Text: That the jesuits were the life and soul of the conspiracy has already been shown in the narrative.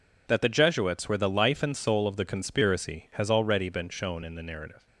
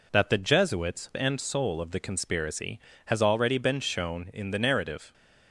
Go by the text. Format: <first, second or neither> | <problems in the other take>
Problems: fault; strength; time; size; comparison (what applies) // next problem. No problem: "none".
first | skips "were the life"; at 1.1 s